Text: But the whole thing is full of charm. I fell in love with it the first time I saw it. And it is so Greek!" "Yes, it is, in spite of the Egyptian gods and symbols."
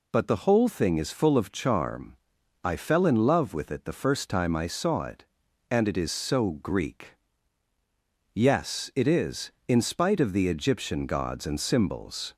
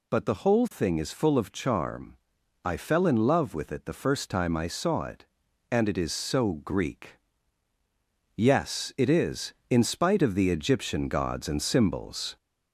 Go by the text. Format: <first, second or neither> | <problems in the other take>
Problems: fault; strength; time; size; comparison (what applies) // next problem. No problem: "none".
first | gets louder; slight; throughout; 3 dB